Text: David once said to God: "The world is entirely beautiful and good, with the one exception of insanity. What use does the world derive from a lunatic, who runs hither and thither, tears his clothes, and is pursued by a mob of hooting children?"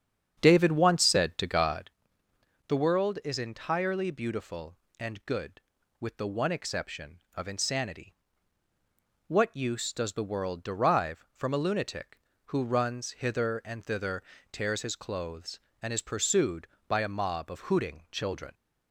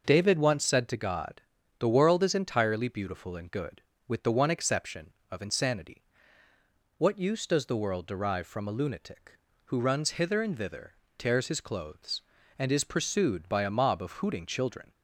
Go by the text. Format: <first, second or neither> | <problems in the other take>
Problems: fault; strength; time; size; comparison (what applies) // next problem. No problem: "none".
second | starts louder than the rest; strong; until 2.0 s; 8 dB